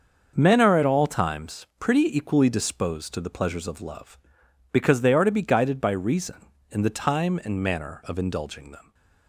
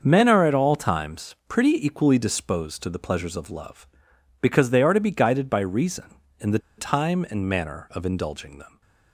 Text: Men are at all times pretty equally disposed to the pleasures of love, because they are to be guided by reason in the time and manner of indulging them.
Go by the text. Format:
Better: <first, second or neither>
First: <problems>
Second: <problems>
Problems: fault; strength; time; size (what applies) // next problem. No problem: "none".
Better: first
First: starts louder than the rest; until 1.3 s; 6.5 dB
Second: starts louder than the rest; until 1.0 s; 6.5 dB // pauses between "the" and "time"; slight; at 6.5 s; 0.19 s long